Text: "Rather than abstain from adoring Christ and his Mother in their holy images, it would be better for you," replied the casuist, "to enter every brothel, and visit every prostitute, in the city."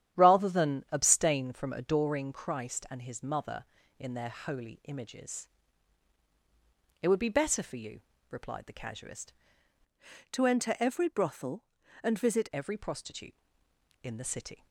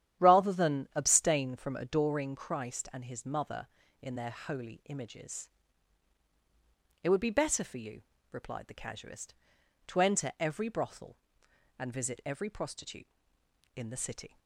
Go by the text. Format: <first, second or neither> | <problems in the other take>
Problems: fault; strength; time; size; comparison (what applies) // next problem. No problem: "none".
second | starts louder than the rest; strong; until 1.2 s; 10.5 dB; strong in the second // changes voice from "to" to "visit"; from 10.3 to 12.4 s; 2.1 s long